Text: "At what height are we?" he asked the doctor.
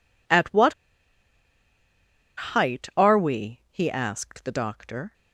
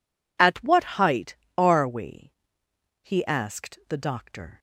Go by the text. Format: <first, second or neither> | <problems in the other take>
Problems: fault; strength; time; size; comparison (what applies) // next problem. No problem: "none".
second | pauses between "what" and "height"; strong; at 0.7 s; 1.7 s long